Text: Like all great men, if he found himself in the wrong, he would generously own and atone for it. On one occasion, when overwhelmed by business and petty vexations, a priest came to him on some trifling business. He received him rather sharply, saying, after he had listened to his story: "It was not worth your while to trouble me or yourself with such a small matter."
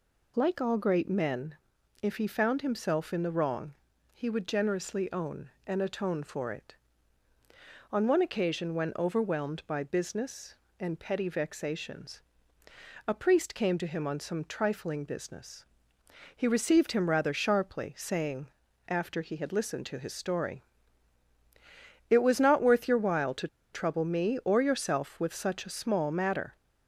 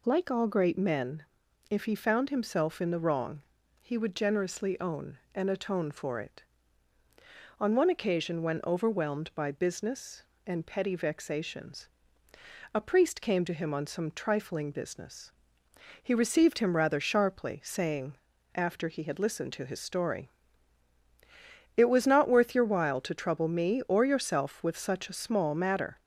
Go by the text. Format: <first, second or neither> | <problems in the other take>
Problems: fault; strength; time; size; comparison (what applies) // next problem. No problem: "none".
second | pauses between "to" and "trouble"; slight; at 23.4 s; 0.25 s long